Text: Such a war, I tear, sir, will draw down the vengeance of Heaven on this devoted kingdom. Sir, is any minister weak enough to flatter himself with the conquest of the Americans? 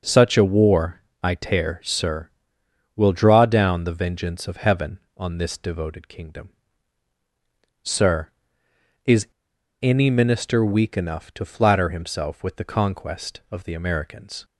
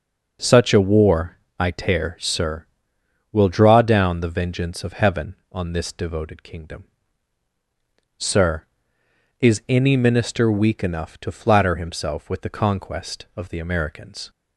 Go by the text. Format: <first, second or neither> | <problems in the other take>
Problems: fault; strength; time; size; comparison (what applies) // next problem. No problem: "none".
second | pauses between "is" and "any"; noticeable; at 9.2 s; 0.54 s long